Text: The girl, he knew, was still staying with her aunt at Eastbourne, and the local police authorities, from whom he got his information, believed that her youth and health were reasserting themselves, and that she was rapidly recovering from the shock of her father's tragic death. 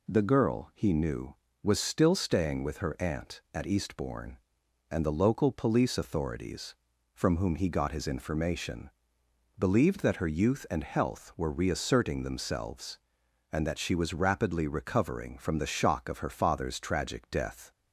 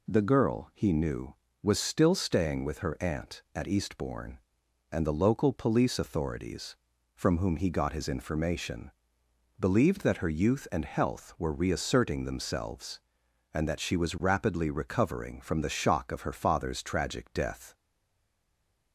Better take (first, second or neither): first